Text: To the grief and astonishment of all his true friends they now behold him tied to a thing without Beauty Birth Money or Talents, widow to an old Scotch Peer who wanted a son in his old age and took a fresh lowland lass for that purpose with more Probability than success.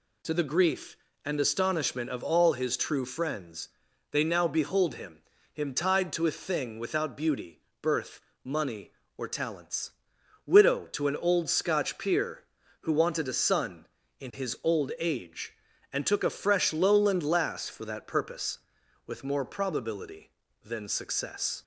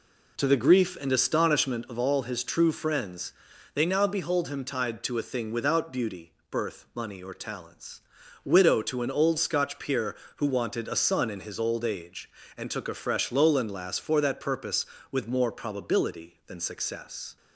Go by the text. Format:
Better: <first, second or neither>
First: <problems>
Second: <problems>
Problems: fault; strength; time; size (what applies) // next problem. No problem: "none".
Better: second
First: pauses between "friends" and "they"; at 3.6 s; 0.42 s long // says "him" twice; at 5.5 s // pauses between "Beauty" and "Birth"; slight; at 7.6 s; 0.22 s long // pauses between "Birth" and "Money"; slight; at 8.2 s; 0.24 s long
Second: pauses between "friends" and "they"; at 3.3 s; 0.44 s long // pauses between "Beauty" and "Birth"; slight; at 6.3 s; 0.18 s long